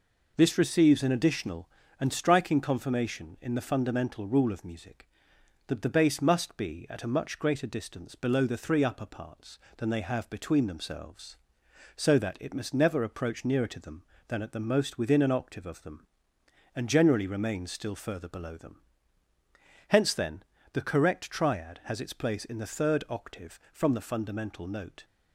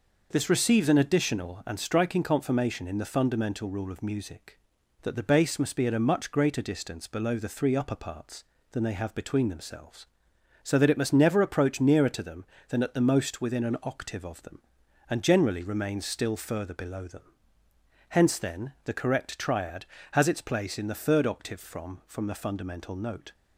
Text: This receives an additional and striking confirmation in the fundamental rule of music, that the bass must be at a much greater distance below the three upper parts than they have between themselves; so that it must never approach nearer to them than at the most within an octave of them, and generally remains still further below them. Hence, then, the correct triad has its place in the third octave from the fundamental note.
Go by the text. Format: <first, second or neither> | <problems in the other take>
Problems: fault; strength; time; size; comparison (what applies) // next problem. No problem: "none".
first | says "from" twice; at 22.0 s